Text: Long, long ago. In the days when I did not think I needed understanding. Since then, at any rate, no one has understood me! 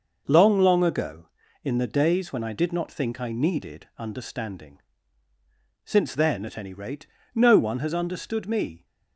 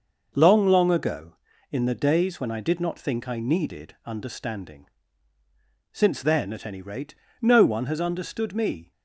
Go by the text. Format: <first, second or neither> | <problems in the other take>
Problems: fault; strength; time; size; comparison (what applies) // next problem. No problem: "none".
neither | none